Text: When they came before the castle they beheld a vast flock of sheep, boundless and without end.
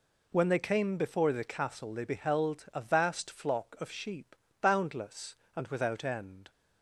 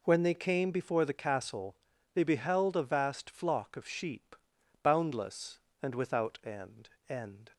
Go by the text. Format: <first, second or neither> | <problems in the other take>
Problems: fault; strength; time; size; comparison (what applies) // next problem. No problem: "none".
first | pauses between "castle" and "they"; at 1.7 s; 0.38 s long // says "end" twice; at 7.0 s